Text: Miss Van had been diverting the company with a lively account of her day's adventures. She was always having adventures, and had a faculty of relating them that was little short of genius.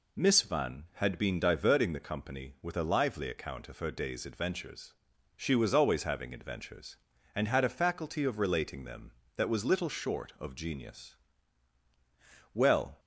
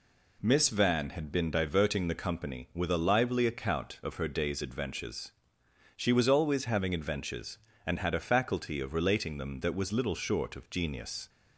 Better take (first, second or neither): second